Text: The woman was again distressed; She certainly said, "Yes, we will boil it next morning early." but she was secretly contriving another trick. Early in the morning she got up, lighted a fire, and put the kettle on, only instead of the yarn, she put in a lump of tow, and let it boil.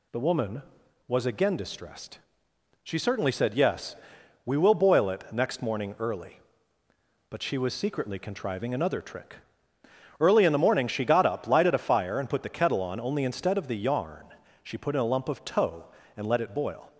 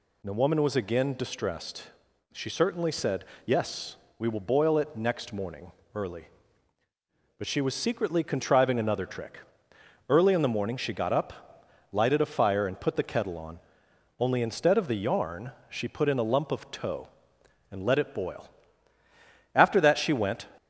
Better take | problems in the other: first | pauses between "morning" and "early"; slight; at 5.7 s; 0.24 s long // goes on to say "After that she went"; noticeable; from 19.5 s on; 0.96 s long

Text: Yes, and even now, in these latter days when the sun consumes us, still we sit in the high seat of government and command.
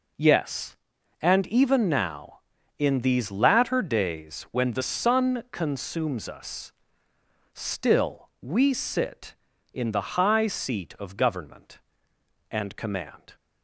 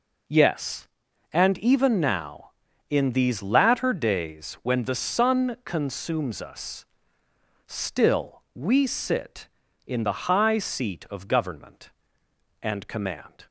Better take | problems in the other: neither | none

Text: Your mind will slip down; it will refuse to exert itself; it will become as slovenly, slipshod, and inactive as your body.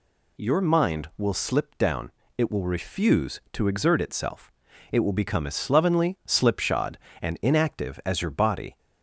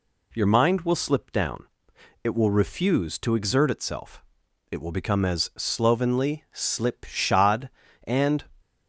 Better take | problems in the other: first | stops before "inactive as your body"; at 8.5 s

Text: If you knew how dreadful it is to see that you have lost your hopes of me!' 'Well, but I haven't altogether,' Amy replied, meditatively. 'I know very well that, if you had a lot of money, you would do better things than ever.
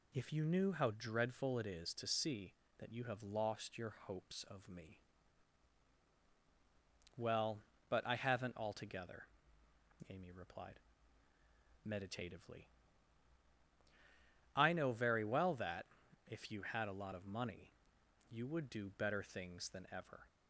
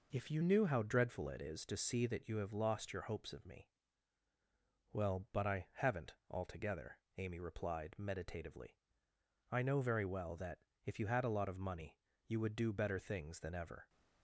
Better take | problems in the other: first | changes voice at "knew"; from 0.4 s on; 13.4 s long

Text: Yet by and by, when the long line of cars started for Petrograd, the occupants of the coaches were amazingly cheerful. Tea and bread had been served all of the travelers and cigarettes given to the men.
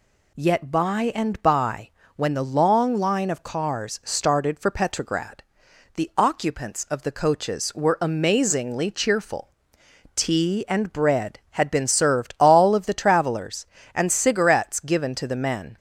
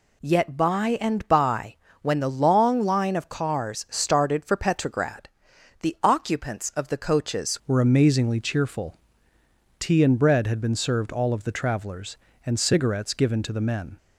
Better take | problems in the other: first | changes voice at "were"; from 7.6 s on; 6.3 s long

